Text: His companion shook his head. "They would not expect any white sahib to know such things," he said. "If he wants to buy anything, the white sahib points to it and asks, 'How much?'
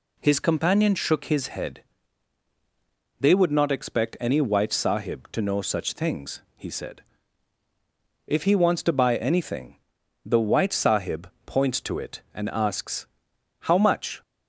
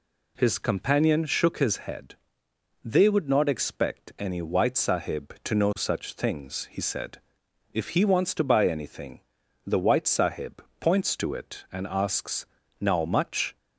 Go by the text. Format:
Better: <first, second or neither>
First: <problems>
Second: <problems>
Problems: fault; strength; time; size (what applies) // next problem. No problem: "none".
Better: first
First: pauses between "sahib" and "points"; slight; at 11.2 s; 0.16 s long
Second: pauses between "sahib" and "points"; slight; at 10.6 s; 0.16 s long // says "Now" for "How"; at 12.7 s